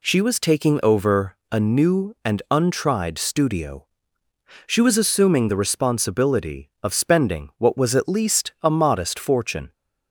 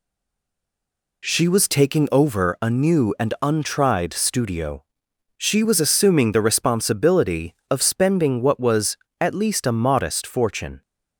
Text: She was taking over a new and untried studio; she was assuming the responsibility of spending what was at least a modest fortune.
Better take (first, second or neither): first